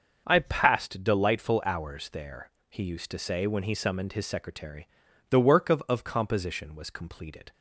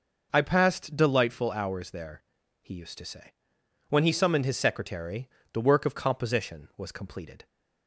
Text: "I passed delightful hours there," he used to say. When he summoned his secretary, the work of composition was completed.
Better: second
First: starts louder than the rest; until 1.2 s; 6.5 dB // says "of" twice; at 5.8 s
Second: none

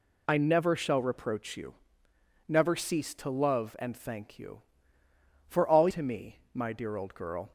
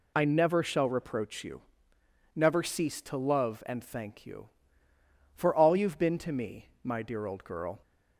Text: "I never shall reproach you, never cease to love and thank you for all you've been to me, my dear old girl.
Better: second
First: skips "you've been"; at 5.8 s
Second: none

